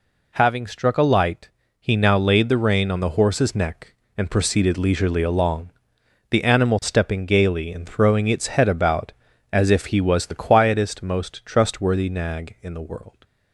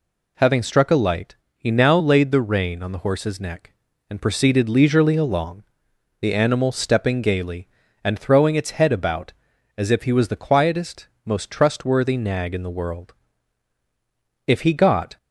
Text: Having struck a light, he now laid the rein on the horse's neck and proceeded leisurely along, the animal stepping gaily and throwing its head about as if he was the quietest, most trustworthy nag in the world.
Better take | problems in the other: first | goes on to say "If he got"; noticeable; from 14.4 s on; 0.70 s long

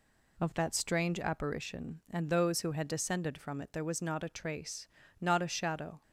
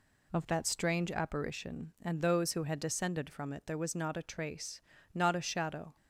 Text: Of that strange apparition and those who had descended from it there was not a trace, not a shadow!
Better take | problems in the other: neither | none

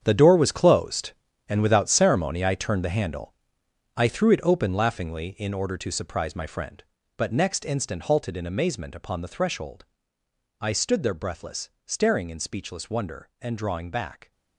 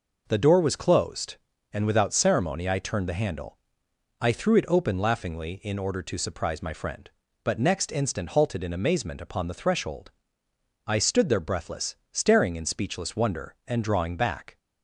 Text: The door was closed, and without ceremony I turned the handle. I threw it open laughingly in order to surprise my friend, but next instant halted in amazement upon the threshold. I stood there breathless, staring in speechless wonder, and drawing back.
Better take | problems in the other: second | gets quieter; strong; throughout; 12 dB

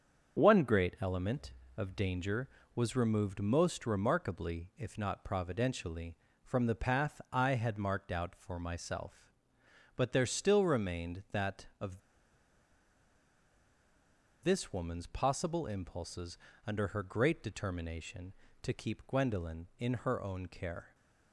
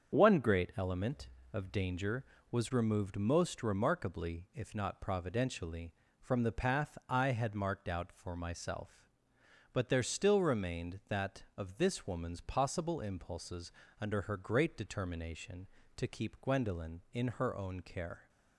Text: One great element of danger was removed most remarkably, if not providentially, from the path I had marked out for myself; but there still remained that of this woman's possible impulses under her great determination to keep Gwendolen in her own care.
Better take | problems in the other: second | starts louder than the rest; strong; until 1.4 s; 7 dB; strong in the second // pauses between "of" and "this"; strong; at 11.9 s; 2.4 s long // pauses between "impulses" and "under"; slight; at 16.3 s; 0.28 s long; slight in the second

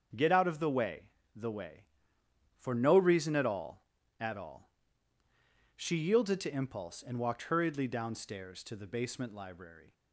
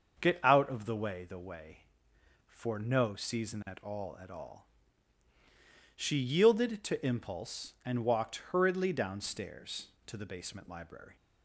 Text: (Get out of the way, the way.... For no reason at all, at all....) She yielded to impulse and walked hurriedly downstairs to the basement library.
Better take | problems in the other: first | starts louder than the rest; until 1.2 s; 6.5 dB; also in the first // says "season" for "reason"; at 3.1 s

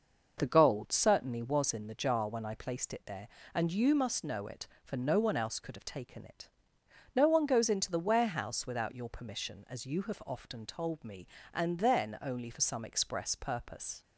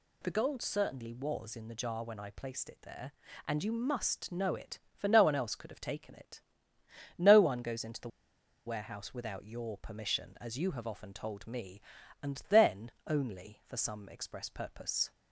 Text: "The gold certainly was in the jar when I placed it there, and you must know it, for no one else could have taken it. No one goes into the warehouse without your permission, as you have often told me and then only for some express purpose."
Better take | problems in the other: first | pauses between "the" and "warehouse"; noticeable; at 8.0 s; 0.57 s long // pauses between "then" and "only"; slight; at 12.9 s; 0.16 s long

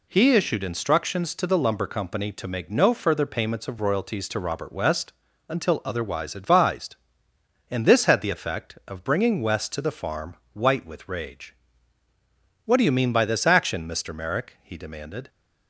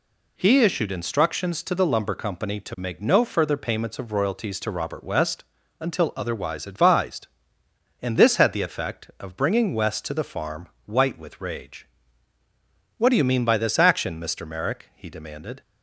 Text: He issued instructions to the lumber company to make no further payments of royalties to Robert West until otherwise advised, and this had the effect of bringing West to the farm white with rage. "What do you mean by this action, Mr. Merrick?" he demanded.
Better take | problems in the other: neither | pauses between "West" and "until"; the same in both // pauses between "farm" and "white"; slight; the same in both

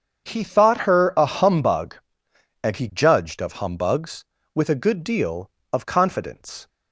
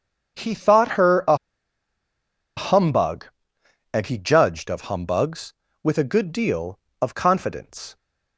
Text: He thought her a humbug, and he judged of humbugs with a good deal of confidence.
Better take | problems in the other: first | starts louder than the rest; strong; until 2.6 s; 7.5 dB; strong in the first // pauses between "a" and "humbug"; at 1.3 s; 1.2 s long

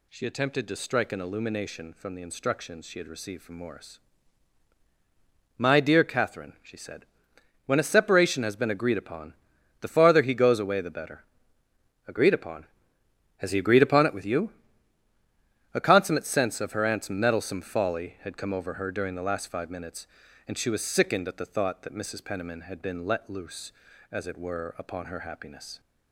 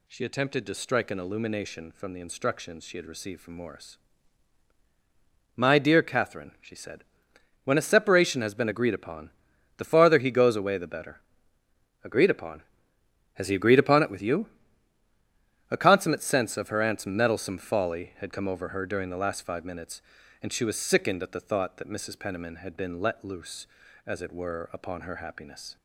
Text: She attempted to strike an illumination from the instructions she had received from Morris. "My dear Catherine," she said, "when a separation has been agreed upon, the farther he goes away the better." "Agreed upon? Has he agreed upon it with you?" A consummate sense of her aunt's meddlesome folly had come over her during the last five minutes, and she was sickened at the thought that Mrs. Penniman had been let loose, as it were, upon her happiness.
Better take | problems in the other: neither | none

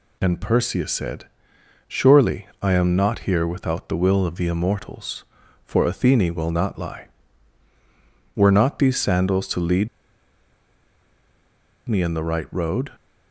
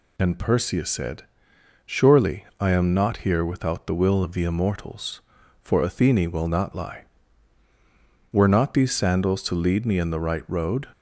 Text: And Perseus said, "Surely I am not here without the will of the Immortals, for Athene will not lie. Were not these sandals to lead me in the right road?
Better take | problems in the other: second | pauses between "Surely" and "I"; slight; at 2.4 s; 0.16 s long; slight in the second // pauses between "lead" and "me"; strong; at 9.8 s; 2.0 s long

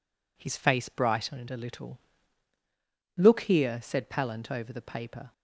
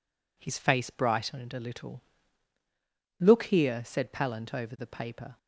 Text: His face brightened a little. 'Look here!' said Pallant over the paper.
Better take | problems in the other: neither | none

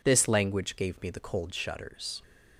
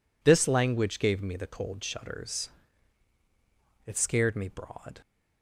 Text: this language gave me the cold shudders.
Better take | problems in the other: first | goes on to say "It scared me broad"; noticeable; from 3.8 s on; 1.1 s long

